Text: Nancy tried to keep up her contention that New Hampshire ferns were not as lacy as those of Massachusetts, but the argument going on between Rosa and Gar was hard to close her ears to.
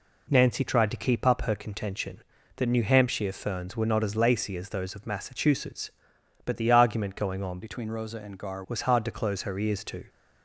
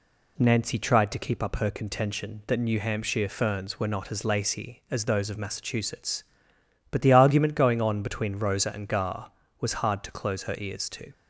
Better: second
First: changes voice from "between" to "Gar"; from 7.6 to 8.6 s; 1.0 s long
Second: none

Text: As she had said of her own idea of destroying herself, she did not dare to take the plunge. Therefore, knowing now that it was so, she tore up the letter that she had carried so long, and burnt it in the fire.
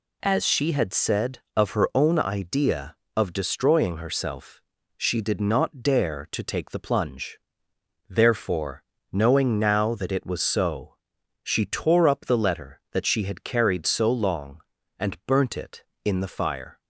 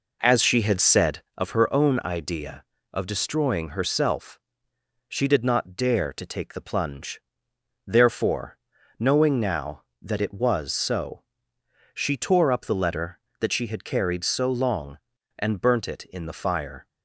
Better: first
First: none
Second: starts louder than the rest; noticeable; until 1.4 s; 4.5 dB

